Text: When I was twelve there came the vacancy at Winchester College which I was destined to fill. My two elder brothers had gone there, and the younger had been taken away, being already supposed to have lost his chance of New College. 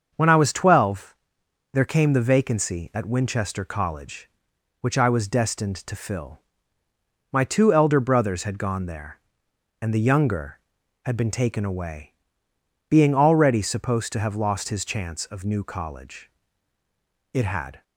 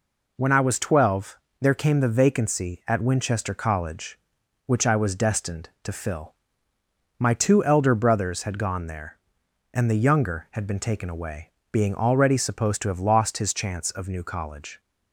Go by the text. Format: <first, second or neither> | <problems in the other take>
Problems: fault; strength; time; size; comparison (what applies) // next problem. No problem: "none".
second | starts louder than the rest; until 1.1 s; 6.5 dB // pauses between "twelve" and "there"; noticeable; at 1.1 s; 0.58 s long; slight in the second // goes on to say "It had"; from 17.3 s on; 0.50 s long